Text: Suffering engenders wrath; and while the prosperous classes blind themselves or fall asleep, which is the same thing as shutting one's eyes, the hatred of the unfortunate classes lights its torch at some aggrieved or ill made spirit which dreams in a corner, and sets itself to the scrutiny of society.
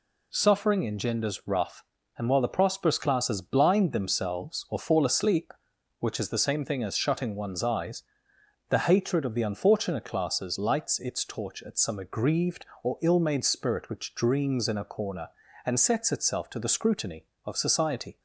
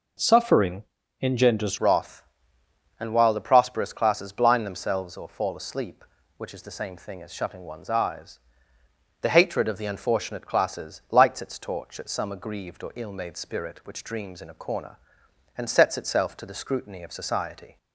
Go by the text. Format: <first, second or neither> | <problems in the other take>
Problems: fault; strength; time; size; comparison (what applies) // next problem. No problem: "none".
first | pauses between "Suffering" and "engenders"; at 0.8 s; 0.40 s long // changes voice at "wrath"; from 1.7 s on; 16.0 s long